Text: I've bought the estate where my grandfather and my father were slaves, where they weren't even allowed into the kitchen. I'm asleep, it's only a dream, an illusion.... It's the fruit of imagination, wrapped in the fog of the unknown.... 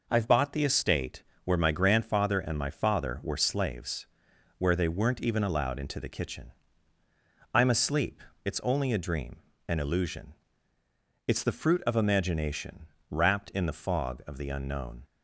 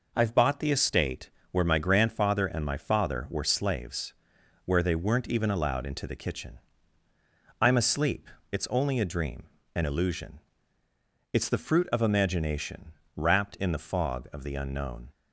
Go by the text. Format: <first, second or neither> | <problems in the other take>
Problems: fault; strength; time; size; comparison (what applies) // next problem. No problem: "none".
neither | pauses between "estate" and "where"; slight; the same in both